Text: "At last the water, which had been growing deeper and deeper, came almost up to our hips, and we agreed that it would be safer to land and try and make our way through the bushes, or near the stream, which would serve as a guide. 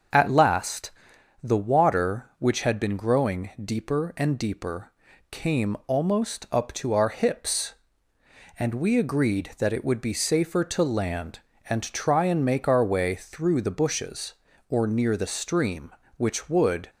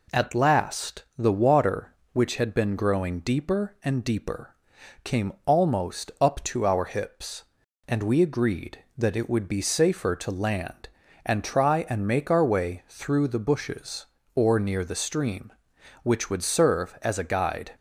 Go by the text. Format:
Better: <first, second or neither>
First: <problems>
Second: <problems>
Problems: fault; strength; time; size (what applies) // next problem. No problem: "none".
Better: second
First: starts louder than the rest; until 1.6 s; 6.5 dB // pauses between "last" and "the"; noticeable; at 0.8 s; 0.54 s long // stops before "serve as a guide"; at 16.8 s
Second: pauses between "last" and "the"; slight; at 1.0 s; 0.16 s long